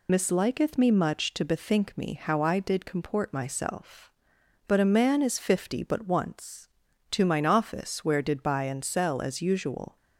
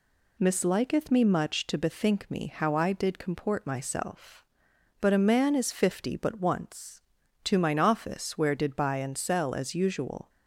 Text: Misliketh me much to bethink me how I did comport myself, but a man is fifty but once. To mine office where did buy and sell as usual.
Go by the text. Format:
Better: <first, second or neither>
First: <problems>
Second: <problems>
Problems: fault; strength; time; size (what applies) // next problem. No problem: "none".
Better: second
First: loses the start of "Misliketh"; at 0.0 s; 35 ms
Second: none